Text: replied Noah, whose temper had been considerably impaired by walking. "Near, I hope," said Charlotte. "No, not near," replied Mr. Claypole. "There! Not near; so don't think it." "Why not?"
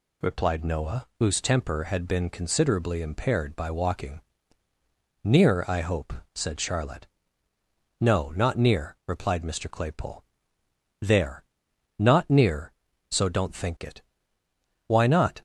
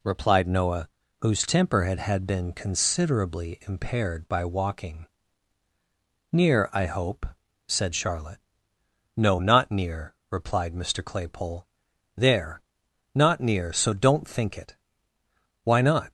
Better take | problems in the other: first | says "had" twice; at 1.9 s

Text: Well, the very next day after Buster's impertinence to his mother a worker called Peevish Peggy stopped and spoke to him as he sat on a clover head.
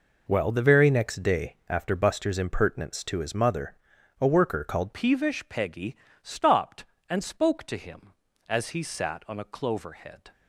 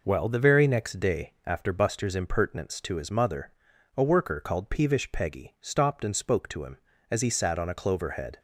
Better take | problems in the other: second | pauses between "mother" and "a"; at 3.7 s; 0.44 s long; also in the second // changes voice at "Peevish"; from 4.9 s on; 5.4 s long // pauses between "Peggy" and "stopped"; slight; at 5.9 s; 0.28 s long

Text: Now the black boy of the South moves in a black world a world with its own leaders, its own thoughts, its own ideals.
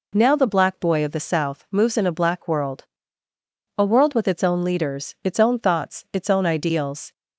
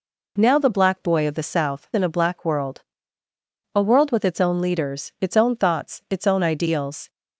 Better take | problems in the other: first | skips "moves"; at 1.9 s // pauses between "world" and "a"; noticeable; at 2.8 s; 0.94 s long; noticeable in the first

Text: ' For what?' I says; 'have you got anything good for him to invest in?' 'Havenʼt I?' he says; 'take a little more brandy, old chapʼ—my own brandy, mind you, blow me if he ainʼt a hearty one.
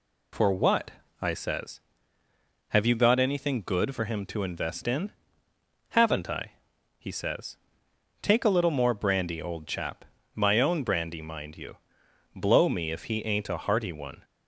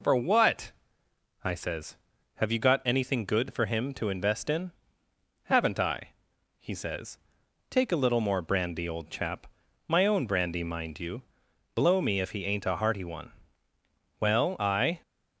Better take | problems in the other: first | goes on to say "Well I"; noticeable; from 14.1 s on; 0.82 s long

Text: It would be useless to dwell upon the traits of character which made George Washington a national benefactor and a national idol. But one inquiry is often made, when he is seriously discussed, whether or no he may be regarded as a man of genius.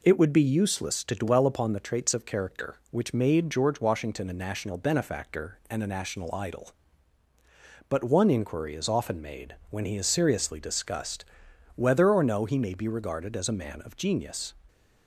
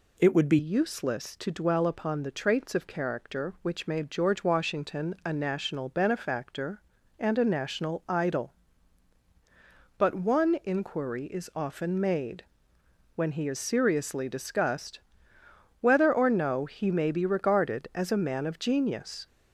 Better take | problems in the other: first | changes voice at "useless"; from 0.5 s on; 18.7 s long

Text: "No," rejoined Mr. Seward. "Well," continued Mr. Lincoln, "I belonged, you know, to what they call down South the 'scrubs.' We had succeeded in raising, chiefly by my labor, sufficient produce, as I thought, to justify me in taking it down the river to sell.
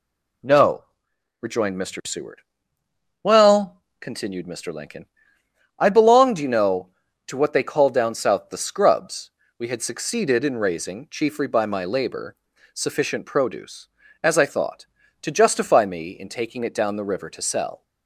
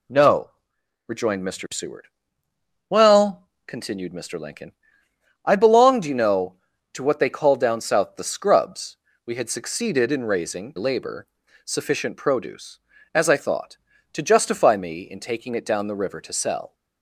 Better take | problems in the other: first | skips "chiefly by my"; at 10.7 s

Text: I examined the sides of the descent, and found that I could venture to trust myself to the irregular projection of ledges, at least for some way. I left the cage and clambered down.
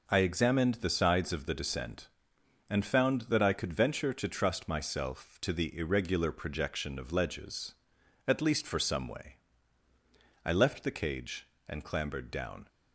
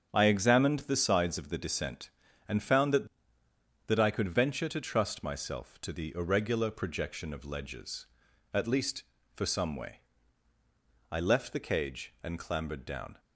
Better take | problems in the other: first | starts louder than the rest; until 1.1 s; 7 dB // says "that" twice; at 3.8 s

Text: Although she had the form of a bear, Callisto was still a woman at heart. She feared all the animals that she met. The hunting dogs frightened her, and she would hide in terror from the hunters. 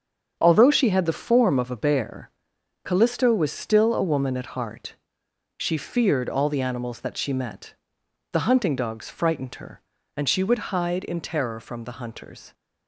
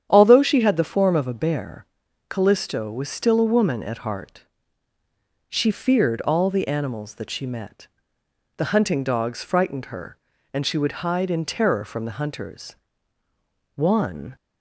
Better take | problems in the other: first | starts louder than the rest; strong; until 1.1 s; 9 dB; strong in the first // goes on to say "One"; from 13.7 s on; 0.60 s long

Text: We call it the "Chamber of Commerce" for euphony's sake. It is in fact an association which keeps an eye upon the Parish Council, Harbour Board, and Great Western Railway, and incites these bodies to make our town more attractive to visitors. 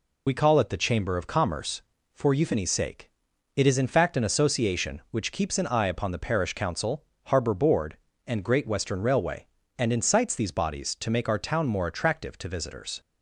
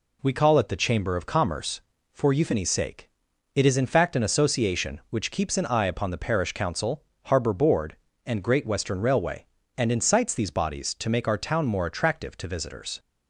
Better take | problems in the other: second | loses the start of "We"; at 0.2 s; 45 ms

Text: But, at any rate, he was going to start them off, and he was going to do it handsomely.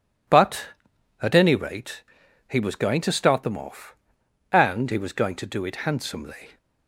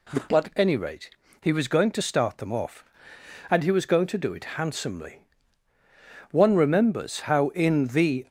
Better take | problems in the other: first | goes on to say "One remembers how in The"; strong; from 6.2 s on; 1.9 s long

